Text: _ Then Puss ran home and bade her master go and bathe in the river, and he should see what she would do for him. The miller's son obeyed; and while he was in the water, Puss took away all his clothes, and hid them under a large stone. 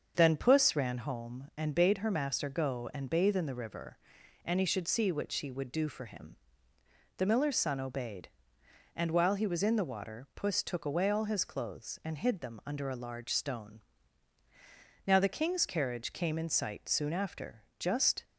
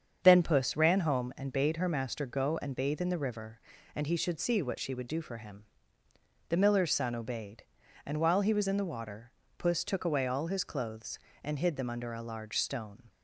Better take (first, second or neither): second